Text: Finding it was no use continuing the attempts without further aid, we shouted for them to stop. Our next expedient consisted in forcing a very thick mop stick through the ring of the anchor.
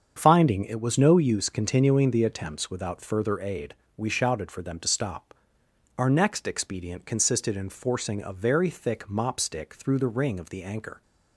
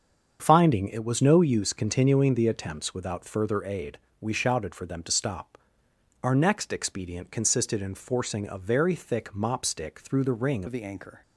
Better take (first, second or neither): first